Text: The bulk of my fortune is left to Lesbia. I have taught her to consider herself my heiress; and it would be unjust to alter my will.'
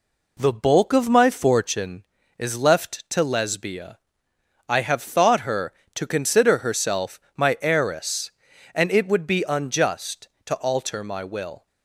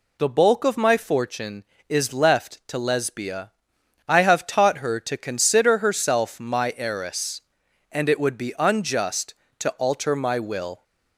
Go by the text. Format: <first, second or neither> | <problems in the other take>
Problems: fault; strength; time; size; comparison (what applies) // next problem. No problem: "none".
second | says "thought" for "taught"; at 5.0 s // pauses between "herself" and "my"; slight; at 7.1 s; 0.18 s long